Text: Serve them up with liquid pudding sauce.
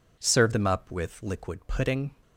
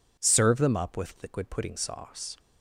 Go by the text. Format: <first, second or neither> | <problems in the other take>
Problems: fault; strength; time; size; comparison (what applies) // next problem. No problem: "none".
second | stops before "sauce"; at 2.2 s